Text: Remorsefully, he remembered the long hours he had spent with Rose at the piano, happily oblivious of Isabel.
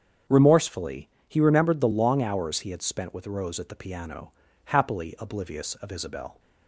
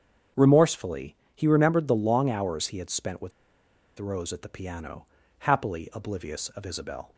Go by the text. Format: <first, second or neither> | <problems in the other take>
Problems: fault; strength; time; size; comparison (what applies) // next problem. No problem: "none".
first | starts louder than the rest; strong; until 1.5 s; 7.5 dB; strong in the first // pauses between "with" and "Rose"; noticeable; at 3.3 s; 0.68 s long